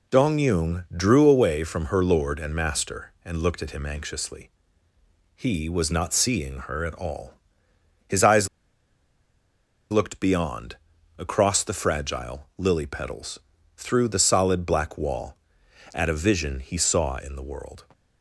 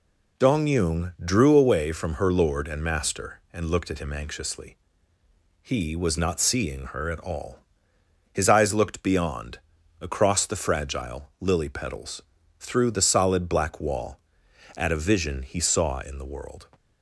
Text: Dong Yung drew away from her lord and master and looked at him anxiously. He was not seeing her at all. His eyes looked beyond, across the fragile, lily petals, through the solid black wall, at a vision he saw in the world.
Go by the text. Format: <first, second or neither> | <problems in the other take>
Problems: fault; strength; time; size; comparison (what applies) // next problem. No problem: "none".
second | pauses between "eyes" and "looked"; strong; at 8.4 s; 1.4 s long